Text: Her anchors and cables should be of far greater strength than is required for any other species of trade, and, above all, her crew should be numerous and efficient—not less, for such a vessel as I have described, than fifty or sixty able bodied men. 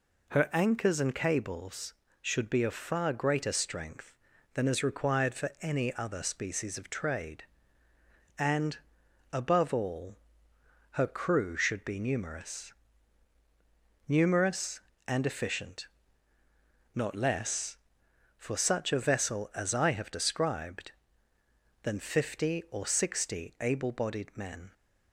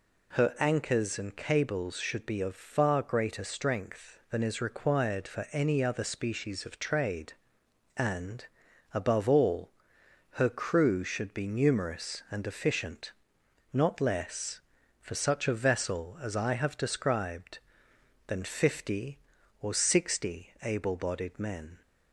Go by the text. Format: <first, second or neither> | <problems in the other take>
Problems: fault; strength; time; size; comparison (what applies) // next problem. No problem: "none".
second | says "numerous" twice; at 14.0 s